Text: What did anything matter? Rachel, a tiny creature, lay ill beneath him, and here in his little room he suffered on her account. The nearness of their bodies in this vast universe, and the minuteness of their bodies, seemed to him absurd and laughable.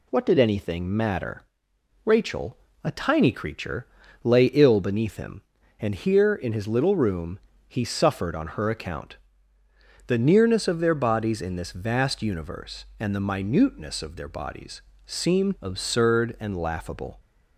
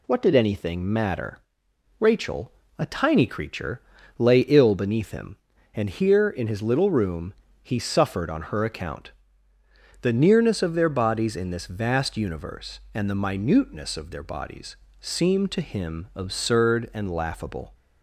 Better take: second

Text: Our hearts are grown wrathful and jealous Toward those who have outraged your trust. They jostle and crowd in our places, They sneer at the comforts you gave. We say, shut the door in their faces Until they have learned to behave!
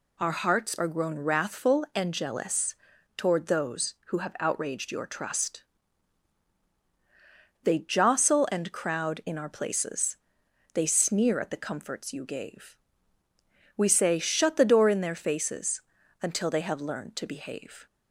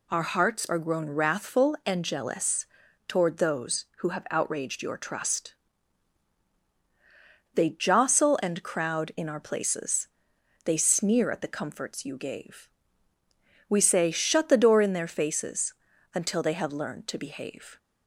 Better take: neither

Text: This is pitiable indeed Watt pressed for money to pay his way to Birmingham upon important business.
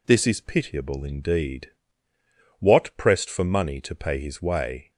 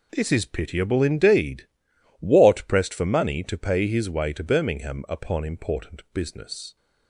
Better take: second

